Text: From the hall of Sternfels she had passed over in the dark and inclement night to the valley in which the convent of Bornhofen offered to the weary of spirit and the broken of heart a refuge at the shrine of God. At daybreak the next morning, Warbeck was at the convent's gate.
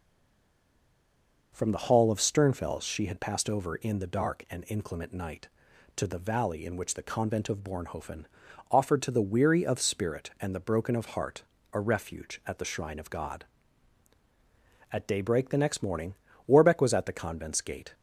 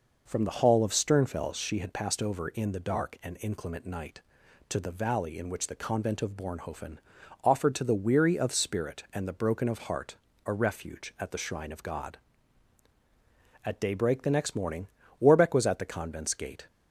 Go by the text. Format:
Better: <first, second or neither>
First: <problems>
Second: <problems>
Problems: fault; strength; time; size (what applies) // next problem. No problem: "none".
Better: second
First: stays silent before the first word; noticeable; until 1.5 s; 1.5 s long // pauses between "Bornhofen" and "offered"; noticeable; at 8.2 s; 0.48 s long // pauses between "heart" and "a"; slight; at 11.4 s; 0.28 s long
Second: pauses between "Bornhofen" and "offered"; noticeable; at 6.9 s; 0.48 s long // pauses between "heart" and "a"; slight; at 10.1 s; 0.28 s long